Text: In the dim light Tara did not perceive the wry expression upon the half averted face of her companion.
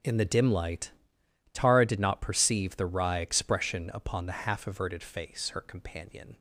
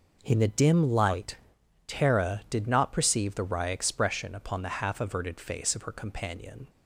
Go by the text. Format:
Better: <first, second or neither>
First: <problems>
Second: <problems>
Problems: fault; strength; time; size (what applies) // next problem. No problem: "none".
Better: second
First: pauses between "light" and "Tara"; noticeable; at 0.8 s; 0.62 s long // skips "of"; at 5.4 s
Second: pauses between "light" and "Tara"; noticeable; at 1.3 s; 0.52 s long